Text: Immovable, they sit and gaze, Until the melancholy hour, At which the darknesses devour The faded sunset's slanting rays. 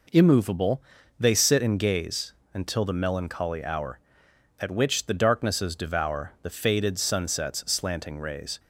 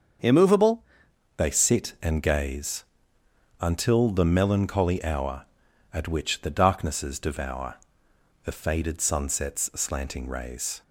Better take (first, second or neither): first